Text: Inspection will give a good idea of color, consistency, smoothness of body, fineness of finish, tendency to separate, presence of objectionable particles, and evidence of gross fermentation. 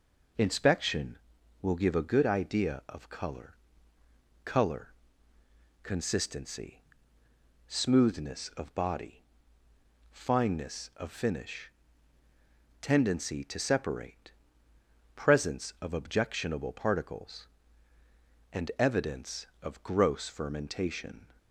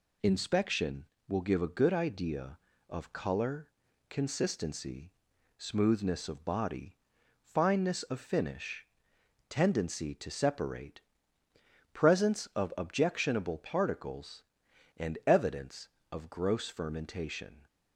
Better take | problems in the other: second | says "color" twice; at 4.4 s

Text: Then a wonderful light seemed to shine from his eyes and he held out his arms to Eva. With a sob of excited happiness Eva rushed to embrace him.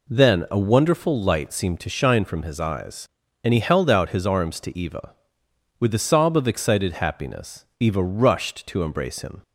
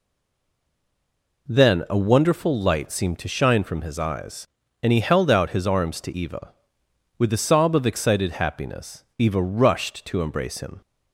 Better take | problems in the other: first | stays silent before the first word; noticeable; until 1.4 s; 1.4 s long // pauses between "happiness" and "Eva"; slight; at 9.0 s; 0.16 s long; slight in the first

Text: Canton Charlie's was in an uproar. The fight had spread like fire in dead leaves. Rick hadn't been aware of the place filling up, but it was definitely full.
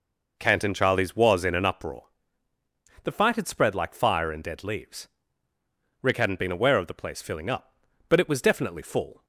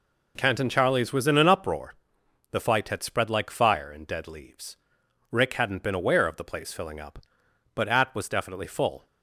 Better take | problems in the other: first | says "at" for "it"; at 7.8 s

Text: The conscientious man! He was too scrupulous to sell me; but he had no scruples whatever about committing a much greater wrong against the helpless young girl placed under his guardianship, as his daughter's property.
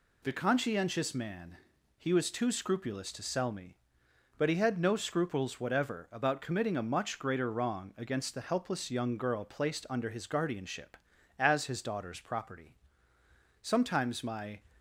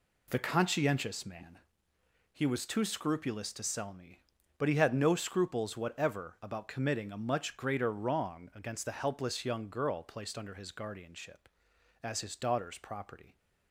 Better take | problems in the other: second | goes on to say "Sometimes my"; noticeable; from 13.6 s on; 0.98 s long

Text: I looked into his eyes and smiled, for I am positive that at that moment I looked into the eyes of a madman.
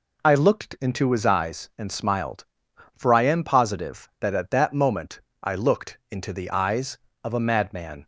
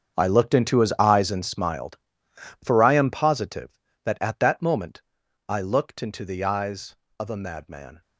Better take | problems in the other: first | gets quieter; strong; throughout; 15.5 dB // pauses between "moment" and "I"; noticeable; at 5.0 s; 0.46 s long; slight in the first

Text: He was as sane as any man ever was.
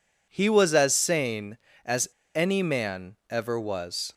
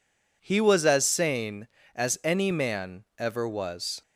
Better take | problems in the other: second | pauses between "as" and "any"; slight; at 2.0 s; 0.26 s long

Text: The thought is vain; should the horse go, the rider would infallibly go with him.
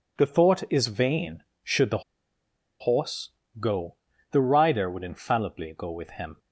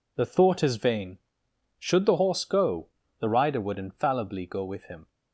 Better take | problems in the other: second | pauses between "the" and "horse"; noticeable; at 2.0 s; 0.79 s long // pauses between "horse" and "go"; slight; at 3.2 s; 0.32 s long

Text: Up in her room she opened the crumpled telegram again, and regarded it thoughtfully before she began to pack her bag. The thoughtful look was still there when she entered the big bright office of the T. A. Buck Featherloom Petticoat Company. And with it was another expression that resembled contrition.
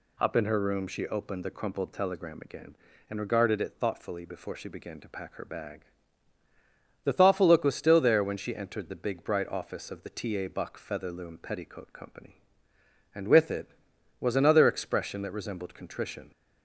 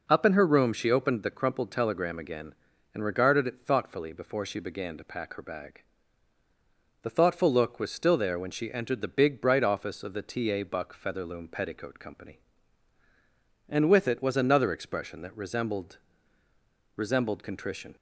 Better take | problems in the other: first | says "resembled" twice; at 16.9 s

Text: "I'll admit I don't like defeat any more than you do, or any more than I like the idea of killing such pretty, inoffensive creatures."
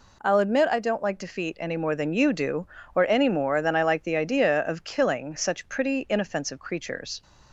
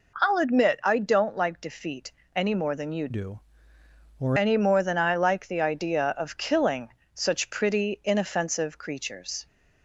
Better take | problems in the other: first | pauses between "defeat" and "any"; slight; at 2.1 s; 0.24 s long // changes voice from "do" to "or"; from 3.1 to 4.3 s; 1.2 s long // pauses between "killing" and "such"; slight; at 6.9 s; 0.24 s long

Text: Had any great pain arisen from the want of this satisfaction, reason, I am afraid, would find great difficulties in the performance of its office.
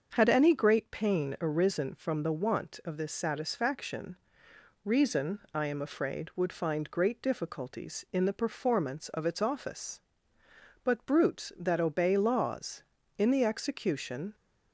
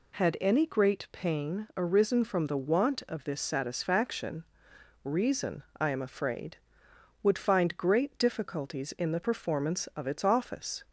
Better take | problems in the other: second | starts louder than the rest; until 1.1 s; 6.5 dB // goes on to say "But brutes that obey laws in the execution"; strong; from 10.8 s on; 3.5 s long

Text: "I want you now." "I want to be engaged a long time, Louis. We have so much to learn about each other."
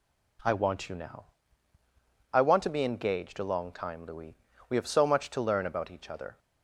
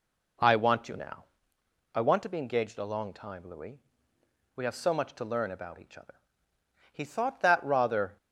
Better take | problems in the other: first | goes on to say "He thought that rather"; noticeable; from 6.9 s on; 1.2 s long

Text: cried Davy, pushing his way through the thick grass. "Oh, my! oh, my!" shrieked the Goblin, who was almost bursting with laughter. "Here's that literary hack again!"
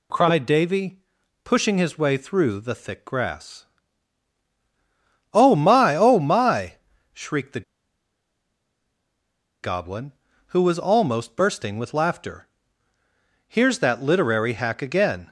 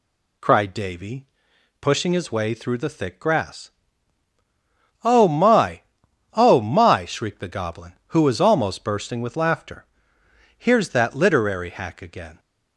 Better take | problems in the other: second | pauses between "the" and "Goblin"; strong; at 7.6 s; 1.9 s long

